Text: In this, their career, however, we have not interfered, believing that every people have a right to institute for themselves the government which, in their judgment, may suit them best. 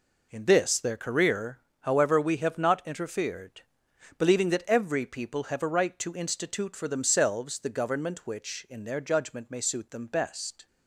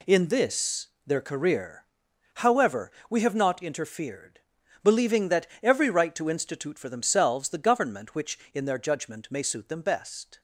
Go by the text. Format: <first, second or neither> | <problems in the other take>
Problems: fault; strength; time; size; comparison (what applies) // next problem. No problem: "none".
first | pauses between "that" and "every"; slight; at 5.4 s; 0.16 s long // skips "people have a"; at 5.8 s